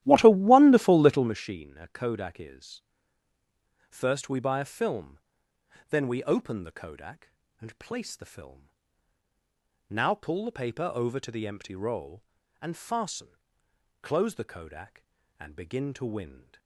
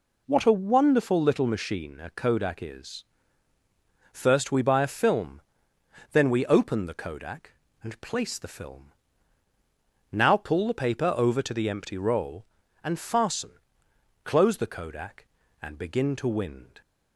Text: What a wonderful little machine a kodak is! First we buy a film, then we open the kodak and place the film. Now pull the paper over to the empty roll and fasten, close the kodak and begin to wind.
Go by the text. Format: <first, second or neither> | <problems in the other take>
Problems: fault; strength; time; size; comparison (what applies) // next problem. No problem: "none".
second | starts louder than the rest; strong; until 1.4 s; 13.5 dB